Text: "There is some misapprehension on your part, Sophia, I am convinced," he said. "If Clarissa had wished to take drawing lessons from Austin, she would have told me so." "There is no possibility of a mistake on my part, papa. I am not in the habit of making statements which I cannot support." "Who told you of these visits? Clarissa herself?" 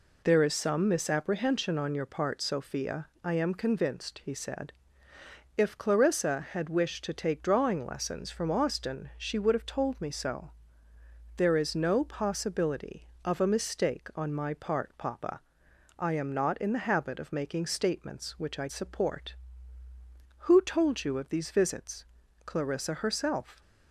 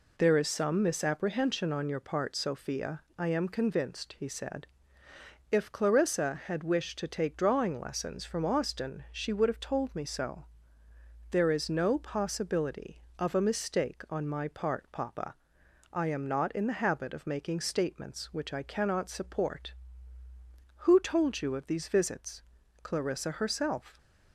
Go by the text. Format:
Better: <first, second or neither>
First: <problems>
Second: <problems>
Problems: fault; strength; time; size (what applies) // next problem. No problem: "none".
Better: second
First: skips "cannot"; at 18.6 s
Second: none